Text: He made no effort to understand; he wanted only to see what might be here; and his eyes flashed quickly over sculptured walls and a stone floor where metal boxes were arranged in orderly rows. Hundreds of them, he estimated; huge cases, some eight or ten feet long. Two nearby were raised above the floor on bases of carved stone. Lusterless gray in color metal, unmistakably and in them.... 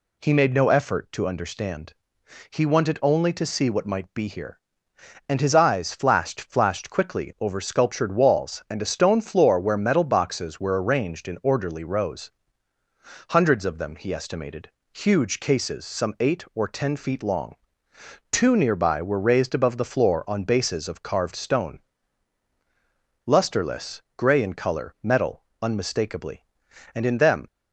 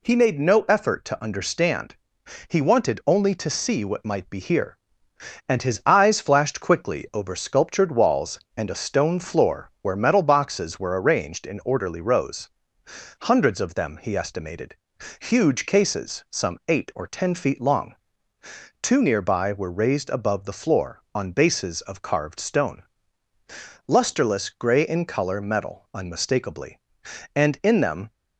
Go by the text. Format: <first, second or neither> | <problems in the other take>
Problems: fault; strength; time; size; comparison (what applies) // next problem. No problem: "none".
second | says "flashed" twice; at 6.4 s // pauses between "Lusterless" and "gray"; slight; at 24.0 s; 0.16 s long